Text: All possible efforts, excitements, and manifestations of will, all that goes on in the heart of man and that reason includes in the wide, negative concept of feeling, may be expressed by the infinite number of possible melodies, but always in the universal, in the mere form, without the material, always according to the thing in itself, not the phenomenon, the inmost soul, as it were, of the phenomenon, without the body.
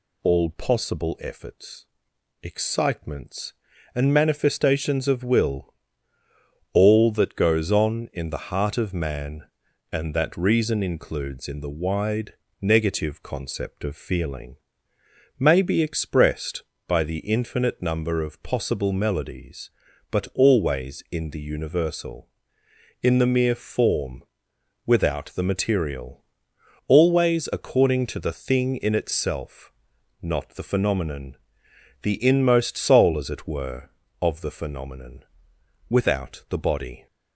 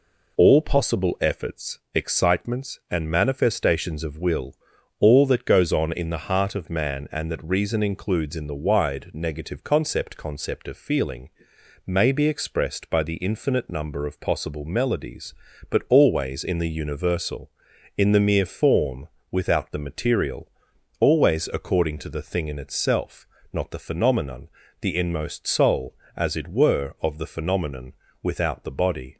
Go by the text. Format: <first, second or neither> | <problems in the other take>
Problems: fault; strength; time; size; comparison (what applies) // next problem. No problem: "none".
first | says "concept" twice; at 10.1 s